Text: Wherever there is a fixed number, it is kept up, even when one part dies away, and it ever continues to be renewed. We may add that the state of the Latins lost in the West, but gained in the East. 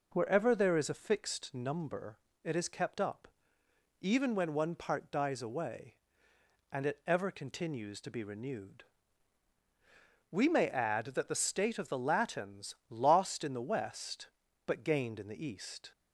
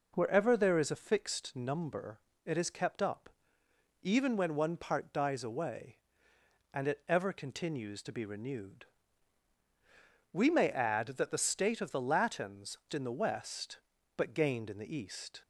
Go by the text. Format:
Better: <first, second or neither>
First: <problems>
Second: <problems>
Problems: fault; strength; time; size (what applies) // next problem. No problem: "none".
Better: first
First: none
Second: skips "lost"; at 12.8 s